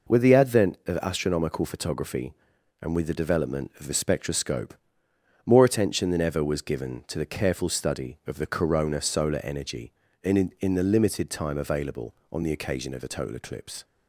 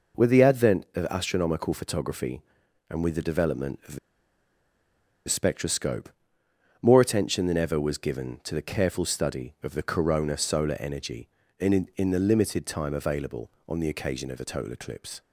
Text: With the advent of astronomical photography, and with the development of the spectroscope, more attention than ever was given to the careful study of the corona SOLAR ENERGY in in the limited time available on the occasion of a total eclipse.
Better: first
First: none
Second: pauses between "the" and "spectroscope"; strong; at 3.9 s; 1.2 s long

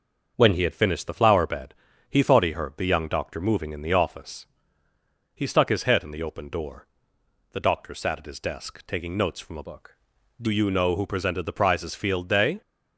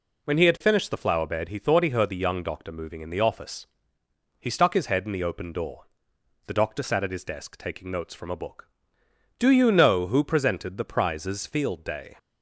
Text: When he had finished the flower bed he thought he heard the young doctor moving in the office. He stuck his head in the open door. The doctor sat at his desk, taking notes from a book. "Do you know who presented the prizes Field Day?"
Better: second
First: starts louder than the rest; until 1.3 s; 6.5 dB // pauses between "bed" and "he"; slight; at 1.7 s; 0.36 s long // changes voice from "book" to "Do"; from 9.6 to 10.4 s; 0.8 s long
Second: none

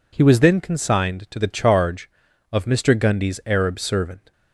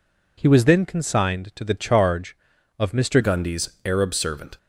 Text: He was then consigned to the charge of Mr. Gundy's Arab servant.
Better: first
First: none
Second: changes voice at "Gundy's"; from 3.2 s on; 1.3 s long

